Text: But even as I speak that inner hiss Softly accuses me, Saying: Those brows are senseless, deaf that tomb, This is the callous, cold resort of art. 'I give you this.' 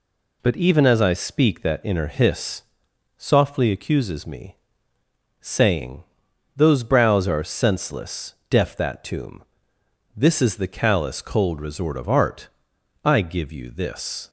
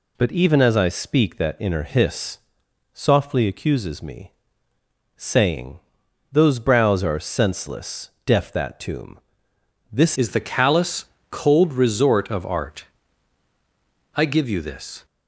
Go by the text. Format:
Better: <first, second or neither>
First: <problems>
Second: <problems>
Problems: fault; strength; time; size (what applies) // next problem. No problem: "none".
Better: first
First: pauses between "hiss" and "Softly"; noticeable; at 2.6 s; 0.56 s long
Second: pauses between "hiss" and "Softly"; noticeable; at 2.3 s; 0.56 s long // changes voice at "is"; from 10.1 s on; 4.9 s long